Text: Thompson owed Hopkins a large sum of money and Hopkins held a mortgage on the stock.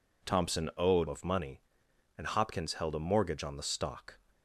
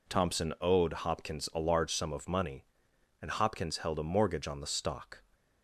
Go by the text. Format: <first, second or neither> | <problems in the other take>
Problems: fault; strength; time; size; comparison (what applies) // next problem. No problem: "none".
second | skips "Hopkins a large sum"; at 1.0 s